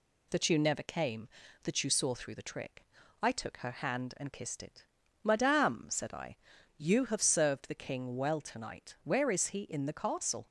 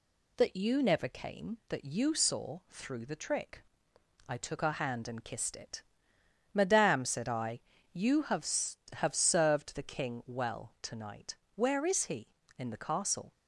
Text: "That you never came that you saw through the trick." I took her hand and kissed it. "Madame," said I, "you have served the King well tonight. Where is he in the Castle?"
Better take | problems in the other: first | says "have" twice; at 8.9 s

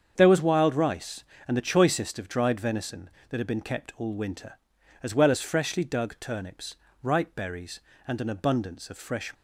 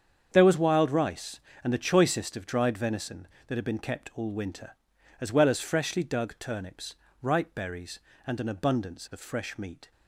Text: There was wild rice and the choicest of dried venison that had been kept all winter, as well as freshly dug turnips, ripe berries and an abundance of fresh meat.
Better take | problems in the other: second | starts louder than the rest; strong; until 1.1 s; 7.5 dB; strong in the second // stops before "meat"; at 9.3 s

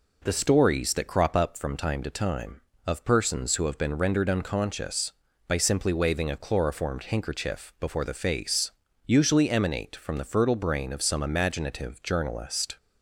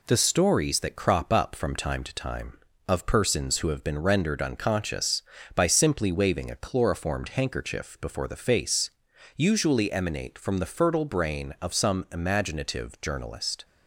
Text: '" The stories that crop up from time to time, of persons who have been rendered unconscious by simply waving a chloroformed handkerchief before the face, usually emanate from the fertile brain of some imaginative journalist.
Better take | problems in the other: neither | none

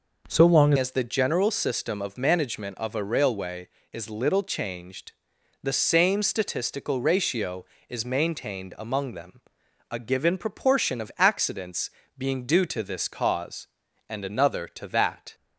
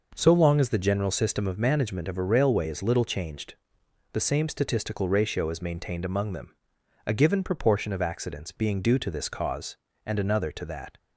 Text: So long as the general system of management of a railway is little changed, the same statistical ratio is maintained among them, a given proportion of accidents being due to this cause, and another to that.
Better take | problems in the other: second | changes voice at "as"; from 0.7 s on; 14.6 s long // pauses between "accidents" and "being"; slight; at 11.9 s; 0.26 s long

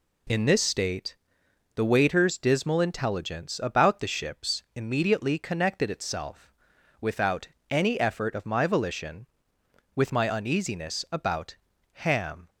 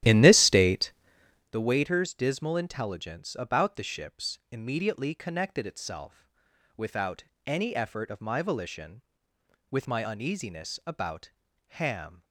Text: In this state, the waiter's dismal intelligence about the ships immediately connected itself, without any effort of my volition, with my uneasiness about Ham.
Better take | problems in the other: first | starts louder than the rest; strong; until 1.6 s; 12.5 dB // pauses between "without" and "any"; slight; at 7.2 s; 0.22 s long; slight in the first // pauses between "about" and "Ham"; noticeable; at 11.2 s; 0.48 s long; noticeable in the first

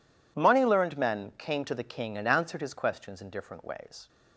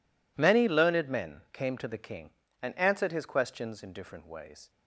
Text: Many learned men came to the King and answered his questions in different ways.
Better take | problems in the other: second | says "Money" for "Many"; at 0.3 s

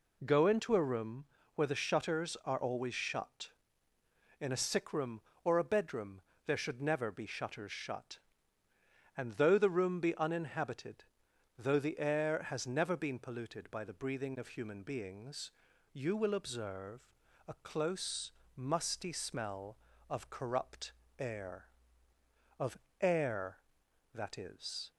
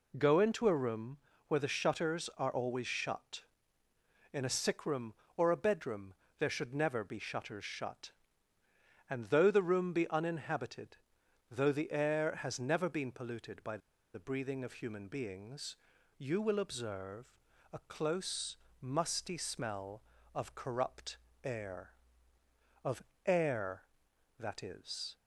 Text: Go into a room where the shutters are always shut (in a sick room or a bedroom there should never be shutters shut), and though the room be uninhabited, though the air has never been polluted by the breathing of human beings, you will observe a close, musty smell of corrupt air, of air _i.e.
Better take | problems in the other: first | pauses between "room" and "where"; slight; at 1.1 s; 0.32 s long; slight in the first // pauses between "bedroom" and "there"; slight; at 6.1 s; 0.26 s long; slight in the first // pauses between "by" and "the"; slight; at 13.7 s; 0.35 s long // pauses between "observe" and "a"; at 17.3 s; 0.40 s long; also in the first // pauses between "corrupt" and "air"; slight; at 21.1 s; 0.26 s long; slight in the first // pauses between "of" and "air"; slight; at 23.0 s; 0.24 s long; slight in the first

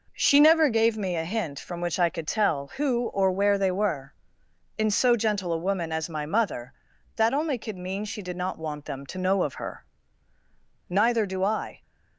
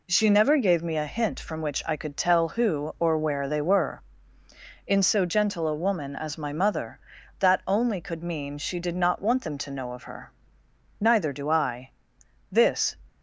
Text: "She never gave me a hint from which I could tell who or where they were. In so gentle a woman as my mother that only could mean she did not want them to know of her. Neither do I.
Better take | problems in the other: first | goes on to say "This"; slight; from 12.5 s on; 0.46 s long

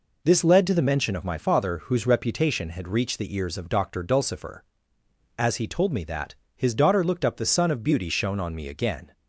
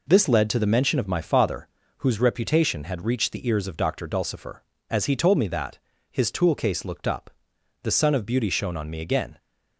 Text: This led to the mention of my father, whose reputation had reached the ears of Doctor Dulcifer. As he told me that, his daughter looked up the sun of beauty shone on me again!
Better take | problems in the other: first | says "toolcase" for "daughter"; at 6.3 s // pauses between "up" and "the"; noticeable; at 7.2 s; 0.54 s long

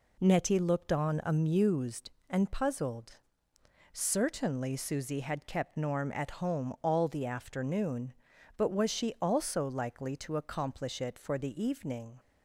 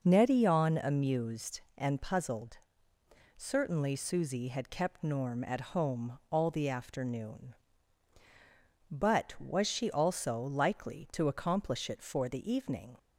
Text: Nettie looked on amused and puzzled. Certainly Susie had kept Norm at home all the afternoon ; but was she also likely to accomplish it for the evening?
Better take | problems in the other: first | skips "looked"; at 0.4 s

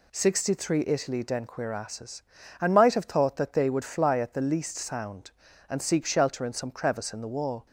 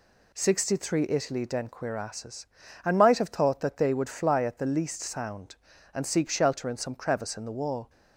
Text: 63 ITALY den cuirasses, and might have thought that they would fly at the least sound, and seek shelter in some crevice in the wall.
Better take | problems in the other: neither | none

